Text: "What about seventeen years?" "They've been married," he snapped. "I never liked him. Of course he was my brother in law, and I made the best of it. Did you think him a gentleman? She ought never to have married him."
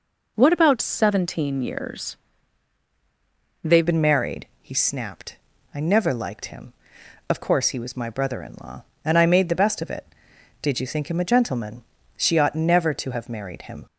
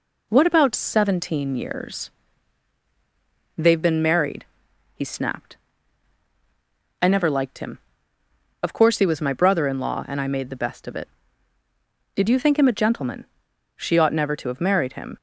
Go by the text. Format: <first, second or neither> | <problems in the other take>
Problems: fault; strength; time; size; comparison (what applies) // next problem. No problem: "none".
second | changes voice at "been"; from 3.8 s on; 10.0 s long